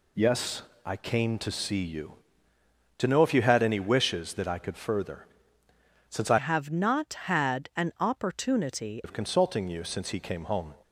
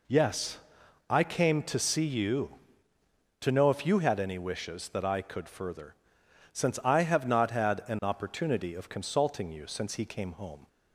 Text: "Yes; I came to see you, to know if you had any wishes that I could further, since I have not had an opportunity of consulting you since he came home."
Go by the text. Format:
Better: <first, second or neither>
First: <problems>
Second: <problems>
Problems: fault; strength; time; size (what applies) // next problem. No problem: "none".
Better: second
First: changes voice from "have" to "opportunity"; from 6.3 to 9.0 s; 2.7 s long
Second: none